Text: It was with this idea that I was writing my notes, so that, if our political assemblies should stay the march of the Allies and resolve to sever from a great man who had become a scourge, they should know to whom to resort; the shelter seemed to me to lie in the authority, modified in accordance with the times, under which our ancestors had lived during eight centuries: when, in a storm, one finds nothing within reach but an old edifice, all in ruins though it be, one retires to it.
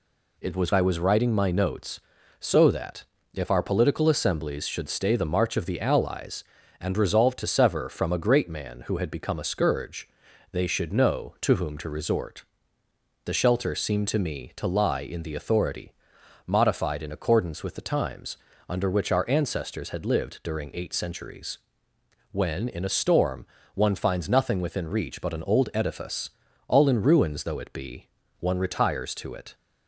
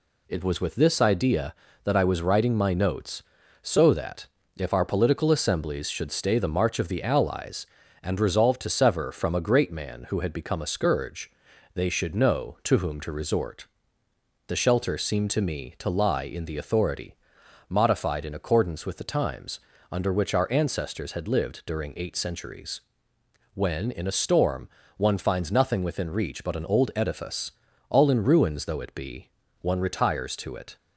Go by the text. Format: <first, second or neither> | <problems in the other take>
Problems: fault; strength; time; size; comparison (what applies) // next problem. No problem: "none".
second | skips "with this idea that"; at 0.7 s